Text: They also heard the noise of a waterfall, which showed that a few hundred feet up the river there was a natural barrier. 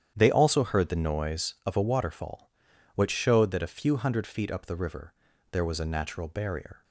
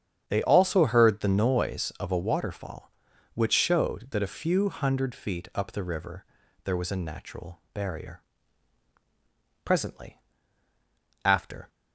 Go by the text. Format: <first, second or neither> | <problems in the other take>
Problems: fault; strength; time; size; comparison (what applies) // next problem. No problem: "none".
first | starts louder than the rest; strong; until 1.2 s; 8.5 dB; strong in the first // pauses between "river" and "there"; at 6.2 s; 0.40 s long; also in the first // goes on to say "Presently after"; strong; from 9.6 s on; 2.0 s long